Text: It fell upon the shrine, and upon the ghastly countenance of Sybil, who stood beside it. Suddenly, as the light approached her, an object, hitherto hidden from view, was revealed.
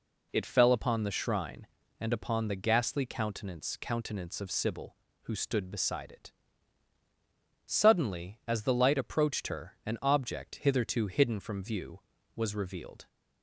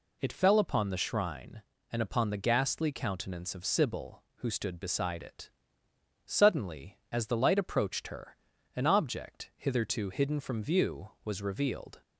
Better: second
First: says "countenance" twice; at 3.8 s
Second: none

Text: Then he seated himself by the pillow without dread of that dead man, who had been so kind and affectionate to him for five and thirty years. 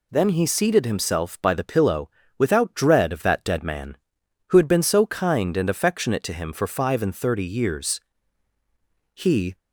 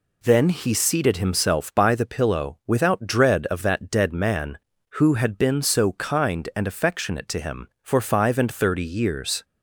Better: second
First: pauses between "pillow" and "without"; slight; at 2.0 s; 0.28 s long // goes on to say "He"; slight; from 9.1 s on; 0.44 s long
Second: none

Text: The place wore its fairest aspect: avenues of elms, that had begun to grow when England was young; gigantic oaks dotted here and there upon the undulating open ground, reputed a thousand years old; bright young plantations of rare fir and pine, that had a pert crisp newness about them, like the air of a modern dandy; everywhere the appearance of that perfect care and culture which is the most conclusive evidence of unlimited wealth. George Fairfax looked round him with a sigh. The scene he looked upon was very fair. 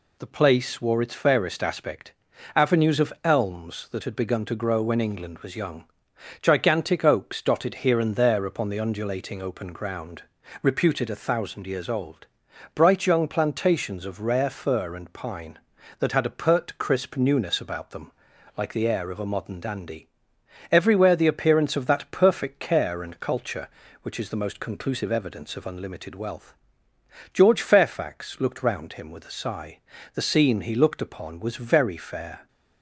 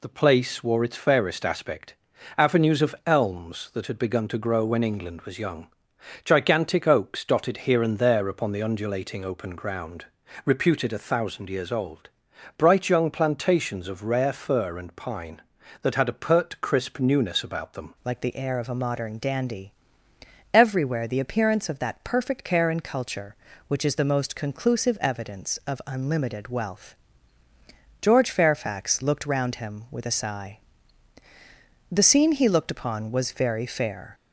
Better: first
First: none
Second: changes voice at "like"; from 18.0 s on; 16.1 s long

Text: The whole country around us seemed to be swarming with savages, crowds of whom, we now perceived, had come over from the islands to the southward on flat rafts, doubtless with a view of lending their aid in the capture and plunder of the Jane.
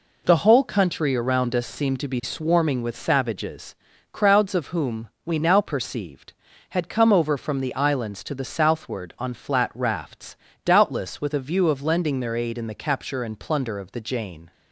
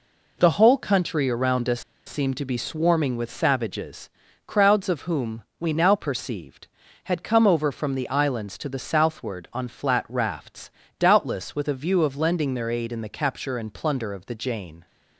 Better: first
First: none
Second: pauses between "us" and "seemed"; slight; at 1.8 s; 0.26 s long

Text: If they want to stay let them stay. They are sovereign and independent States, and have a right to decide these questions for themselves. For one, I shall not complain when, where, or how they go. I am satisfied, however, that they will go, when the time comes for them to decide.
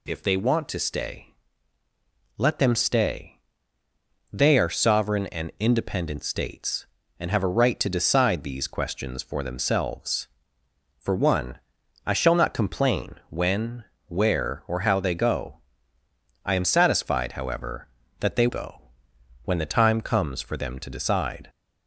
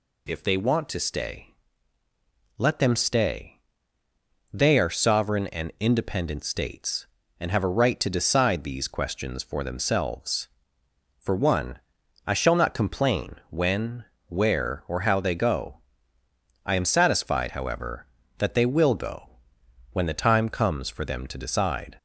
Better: second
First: pauses between "stay" and "let"; at 1.3 s; 1.0 s long // pauses between "complain" and "when"; slight; at 13.1 s; 0.16 s long // skips "will"; at 18.4 s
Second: pauses between "stay" and "let"; at 1.5 s; 1.0 s long // pauses between "complain" and "when"; slight; at 13.3 s; 0.16 s long

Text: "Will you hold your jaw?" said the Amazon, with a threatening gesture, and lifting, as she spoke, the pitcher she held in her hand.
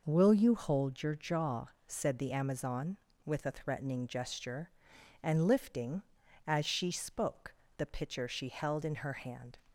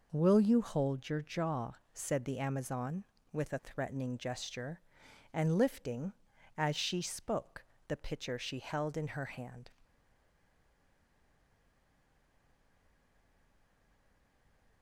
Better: first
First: none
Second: stays silent after the last word; strong; from 9.8 s on; 5.0 s long

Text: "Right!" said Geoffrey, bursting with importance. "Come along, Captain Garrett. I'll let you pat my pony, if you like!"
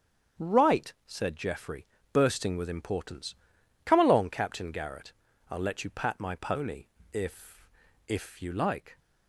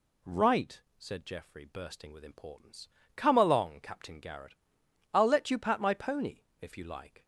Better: second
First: starts louder than the rest; strong; until 1.5 s; 8 dB // says "if" twice; at 8.0 s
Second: none

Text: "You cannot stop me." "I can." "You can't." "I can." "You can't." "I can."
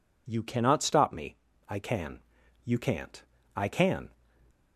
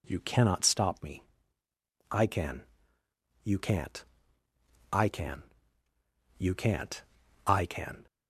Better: second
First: stops before "You can't I can"; at 4.5 s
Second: none

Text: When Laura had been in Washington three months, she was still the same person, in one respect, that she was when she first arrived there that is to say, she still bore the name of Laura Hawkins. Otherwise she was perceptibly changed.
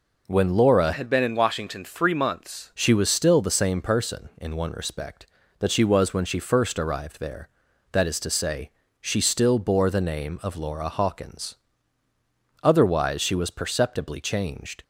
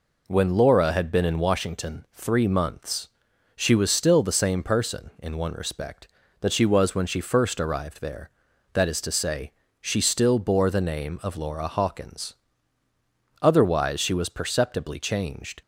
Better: second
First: changes voice from "had" to "months"; from 0.9 to 2.7 s; 1.8 s long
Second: none

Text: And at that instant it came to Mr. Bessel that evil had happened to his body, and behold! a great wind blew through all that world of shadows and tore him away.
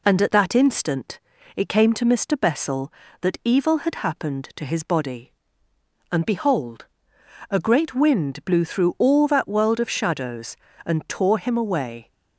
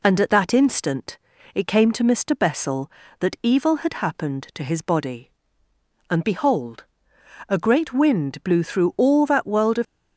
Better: first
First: pauses between "instant" and "it"; slight; at 1.1 s; 0.36 s long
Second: pauses between "instant" and "it"; slight; at 1.1 s; 0.36 s long // stops before "shadows and tore him away"; at 9.8 s

